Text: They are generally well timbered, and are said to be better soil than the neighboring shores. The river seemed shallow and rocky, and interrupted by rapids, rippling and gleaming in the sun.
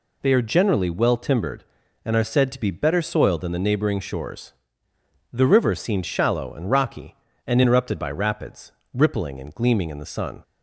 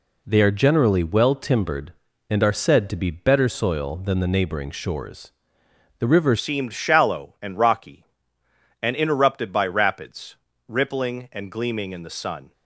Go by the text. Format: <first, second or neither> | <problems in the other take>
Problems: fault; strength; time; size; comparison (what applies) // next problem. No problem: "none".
first | changes voice at "seemed"; from 6.3 s on; 6.2 s long